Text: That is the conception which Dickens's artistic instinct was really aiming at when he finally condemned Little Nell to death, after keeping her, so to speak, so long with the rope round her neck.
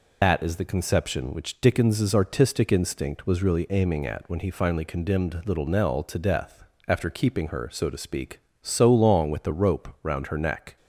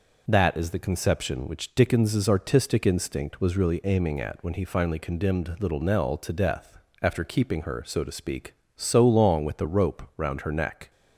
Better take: second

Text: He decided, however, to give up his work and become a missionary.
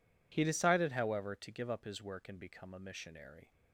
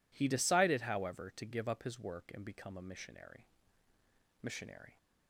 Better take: first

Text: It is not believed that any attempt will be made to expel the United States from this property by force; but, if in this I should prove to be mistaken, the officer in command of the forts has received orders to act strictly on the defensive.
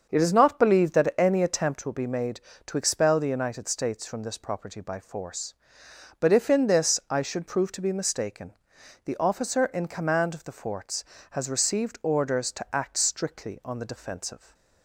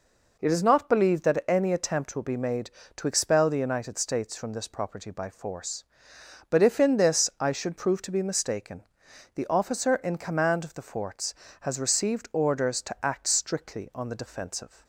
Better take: second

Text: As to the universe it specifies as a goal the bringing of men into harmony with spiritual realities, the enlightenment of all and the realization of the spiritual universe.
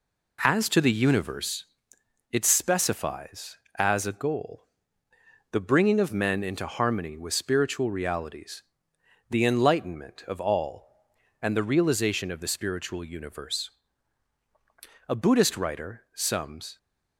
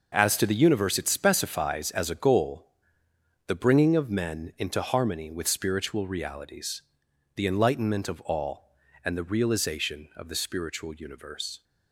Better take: second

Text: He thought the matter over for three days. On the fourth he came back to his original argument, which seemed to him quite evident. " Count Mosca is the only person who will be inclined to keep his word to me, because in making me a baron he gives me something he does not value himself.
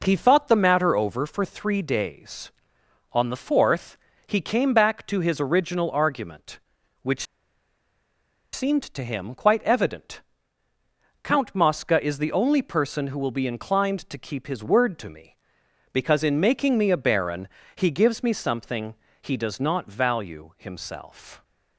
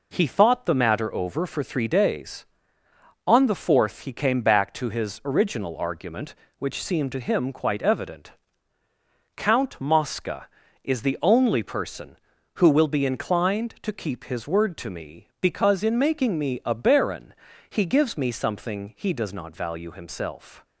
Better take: second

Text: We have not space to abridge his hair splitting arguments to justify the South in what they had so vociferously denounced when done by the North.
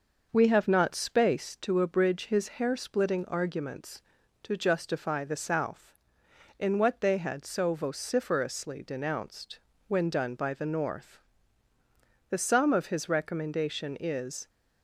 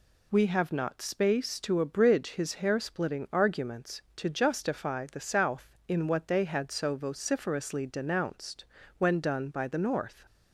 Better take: second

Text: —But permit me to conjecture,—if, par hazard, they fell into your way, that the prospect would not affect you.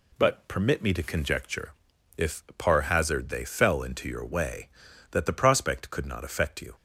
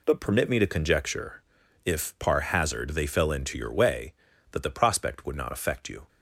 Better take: second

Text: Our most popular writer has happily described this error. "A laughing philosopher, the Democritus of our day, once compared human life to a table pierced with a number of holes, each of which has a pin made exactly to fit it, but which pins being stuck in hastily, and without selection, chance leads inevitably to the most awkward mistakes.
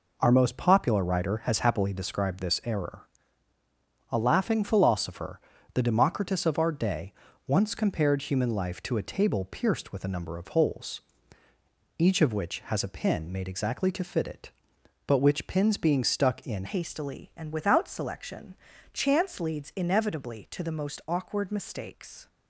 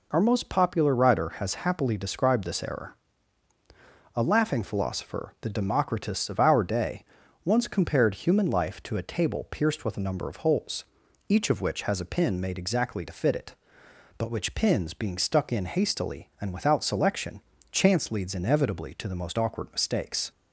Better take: second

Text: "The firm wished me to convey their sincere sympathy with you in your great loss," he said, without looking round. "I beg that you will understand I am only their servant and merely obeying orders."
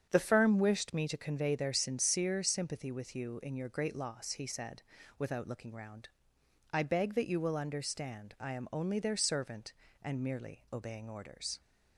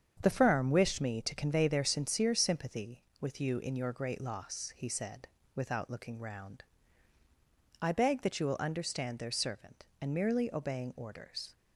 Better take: first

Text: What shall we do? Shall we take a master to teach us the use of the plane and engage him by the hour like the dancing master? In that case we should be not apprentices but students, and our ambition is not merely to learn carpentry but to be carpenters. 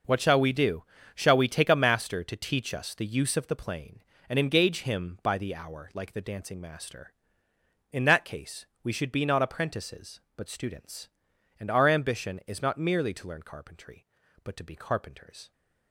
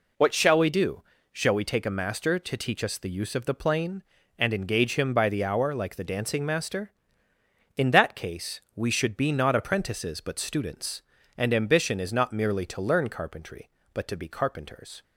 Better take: first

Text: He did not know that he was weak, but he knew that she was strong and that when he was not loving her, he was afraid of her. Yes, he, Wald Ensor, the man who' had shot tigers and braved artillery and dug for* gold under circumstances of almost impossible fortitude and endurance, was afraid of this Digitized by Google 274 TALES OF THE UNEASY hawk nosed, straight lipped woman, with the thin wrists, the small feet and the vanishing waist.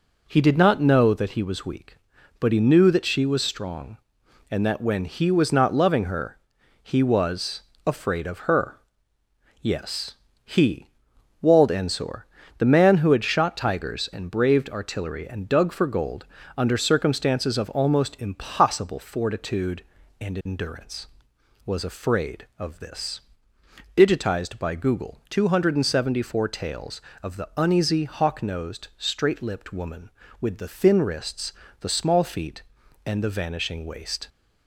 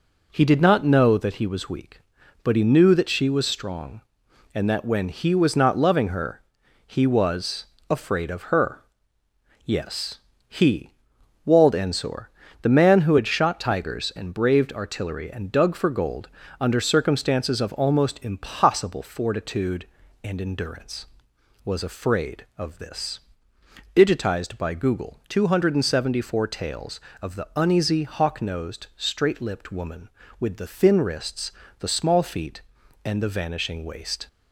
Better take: neither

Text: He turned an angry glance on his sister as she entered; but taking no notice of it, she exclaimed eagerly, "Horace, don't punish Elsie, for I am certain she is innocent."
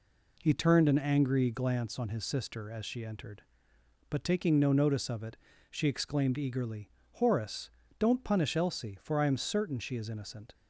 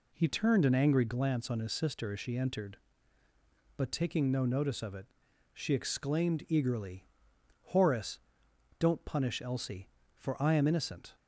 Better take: first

